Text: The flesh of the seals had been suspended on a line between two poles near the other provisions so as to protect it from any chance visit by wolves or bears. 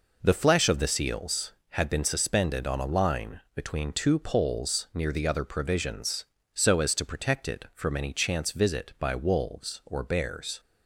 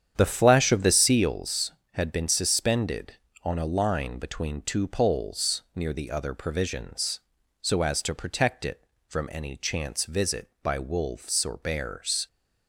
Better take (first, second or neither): first